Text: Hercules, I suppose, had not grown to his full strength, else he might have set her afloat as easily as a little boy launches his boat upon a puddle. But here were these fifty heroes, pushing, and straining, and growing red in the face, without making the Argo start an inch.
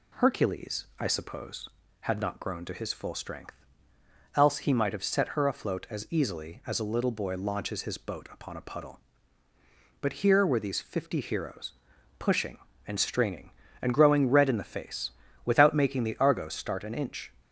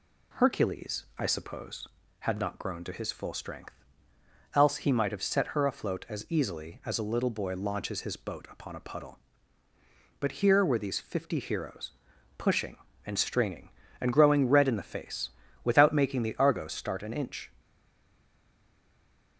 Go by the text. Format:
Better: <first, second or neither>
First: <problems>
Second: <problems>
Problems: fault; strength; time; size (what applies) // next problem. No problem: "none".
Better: first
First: none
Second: stays silent after the last word; noticeable; from 17.5 s on; 1.8 s long